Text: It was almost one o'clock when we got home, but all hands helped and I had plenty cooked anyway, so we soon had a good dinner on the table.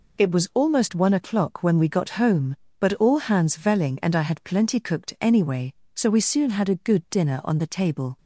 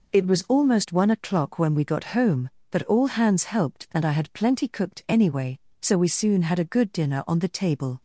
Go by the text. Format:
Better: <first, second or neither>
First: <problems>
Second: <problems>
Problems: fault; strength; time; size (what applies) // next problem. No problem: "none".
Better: second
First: says "velling" for "helped"; at 3.5 s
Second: none